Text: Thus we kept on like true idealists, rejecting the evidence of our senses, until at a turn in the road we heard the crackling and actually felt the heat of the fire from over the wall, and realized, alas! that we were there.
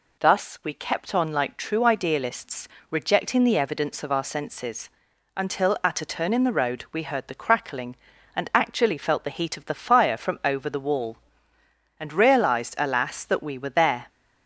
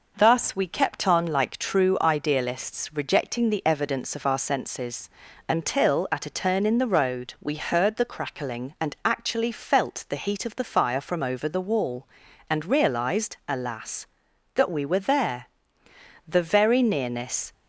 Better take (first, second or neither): first